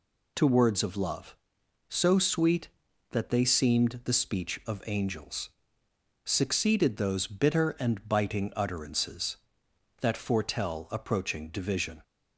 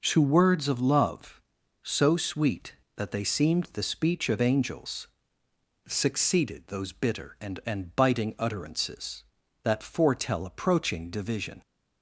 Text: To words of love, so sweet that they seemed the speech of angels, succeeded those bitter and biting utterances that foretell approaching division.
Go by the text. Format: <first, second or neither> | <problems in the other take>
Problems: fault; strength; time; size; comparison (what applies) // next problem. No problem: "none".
first | says "and" twice; at 7.6 s